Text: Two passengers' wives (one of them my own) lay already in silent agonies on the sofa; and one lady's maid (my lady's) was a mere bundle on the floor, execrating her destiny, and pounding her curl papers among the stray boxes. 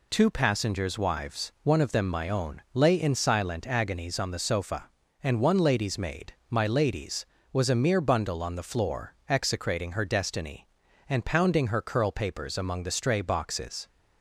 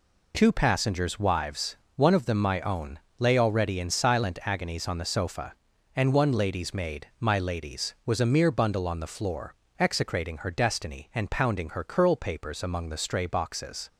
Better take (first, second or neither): second